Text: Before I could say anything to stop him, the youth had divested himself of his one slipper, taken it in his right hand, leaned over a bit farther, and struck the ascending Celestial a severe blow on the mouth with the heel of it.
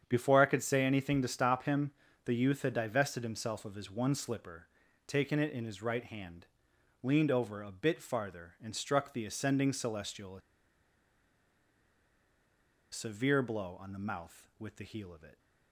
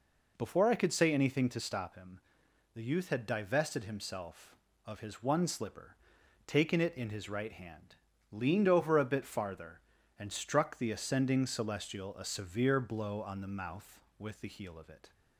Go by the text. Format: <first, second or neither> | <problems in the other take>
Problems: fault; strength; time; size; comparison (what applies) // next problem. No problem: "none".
second | starts louder than the rest; strong; until 1.0 s; 8 dB // pauses between "a" and "severe"; strong; at 10.4 s; 2.5 s long